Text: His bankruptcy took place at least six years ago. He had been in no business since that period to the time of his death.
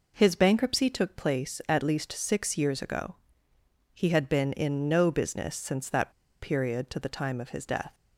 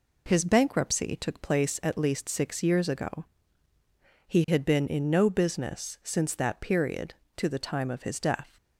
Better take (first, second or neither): second